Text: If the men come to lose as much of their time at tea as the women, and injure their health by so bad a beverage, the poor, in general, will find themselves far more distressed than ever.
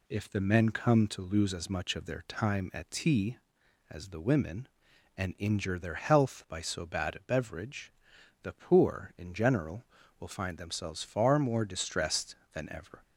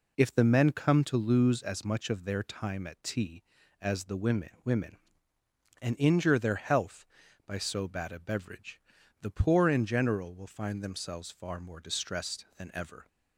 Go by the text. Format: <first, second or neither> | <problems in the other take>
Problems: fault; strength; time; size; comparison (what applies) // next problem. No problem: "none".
first | says "women" twice; at 4.6 s